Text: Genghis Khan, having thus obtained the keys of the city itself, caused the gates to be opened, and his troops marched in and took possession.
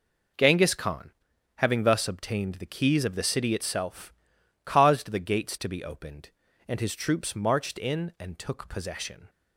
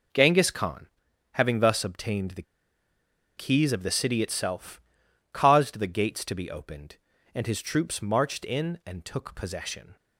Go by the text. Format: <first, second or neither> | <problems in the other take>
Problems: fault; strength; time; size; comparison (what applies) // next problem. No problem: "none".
first | pauses between "the" and "keys"; noticeable; at 2.4 s; 0.94 s long